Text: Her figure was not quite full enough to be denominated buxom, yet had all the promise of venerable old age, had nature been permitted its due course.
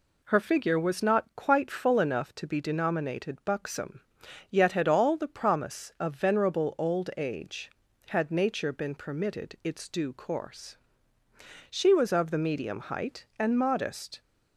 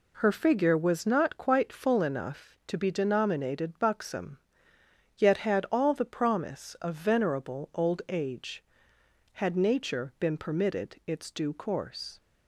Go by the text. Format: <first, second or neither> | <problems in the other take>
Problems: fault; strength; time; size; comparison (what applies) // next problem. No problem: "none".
second | goes on to say "She was of the medium height and modest"; strong; from 11.7 s on; 2.5 s long